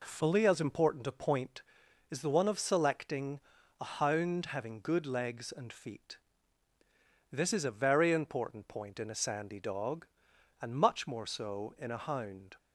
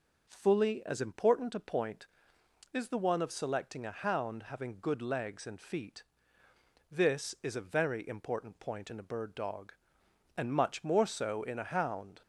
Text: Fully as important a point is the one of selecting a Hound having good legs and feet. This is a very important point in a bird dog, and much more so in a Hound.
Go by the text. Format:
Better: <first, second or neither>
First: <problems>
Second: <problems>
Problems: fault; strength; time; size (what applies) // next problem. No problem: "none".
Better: second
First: pauses between "selecting" and "a"; at 3.3 s; 0.42 s long // says "sandy" for "bird"; at 9.1 s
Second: none